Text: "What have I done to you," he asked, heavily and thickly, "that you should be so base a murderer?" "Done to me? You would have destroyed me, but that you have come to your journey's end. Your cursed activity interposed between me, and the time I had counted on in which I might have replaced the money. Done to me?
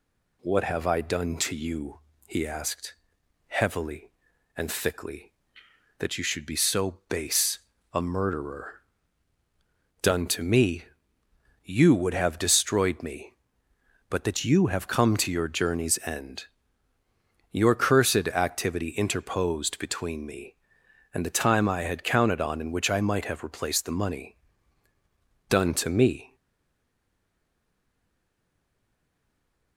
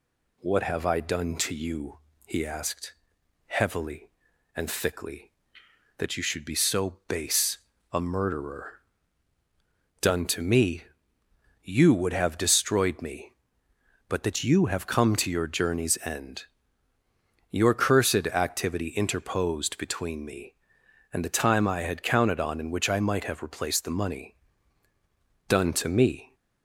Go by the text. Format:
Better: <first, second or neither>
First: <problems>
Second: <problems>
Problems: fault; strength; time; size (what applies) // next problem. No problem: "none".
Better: second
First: pauses between "base" and "a"; slight; at 7.5 s; 0.32 s long // stays silent after the last word; strong; from 26.3 s on; 3.4 s long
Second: pauses between "base" and "a"; slight; at 7.5 s; 0.32 s long